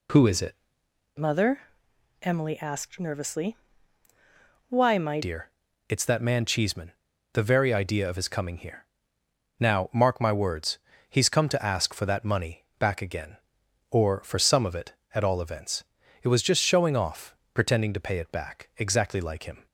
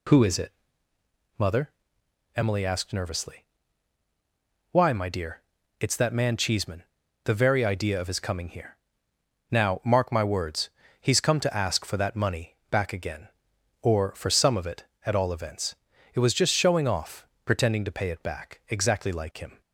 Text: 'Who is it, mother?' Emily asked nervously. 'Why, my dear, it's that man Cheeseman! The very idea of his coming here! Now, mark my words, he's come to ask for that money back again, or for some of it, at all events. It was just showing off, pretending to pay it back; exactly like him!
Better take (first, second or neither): second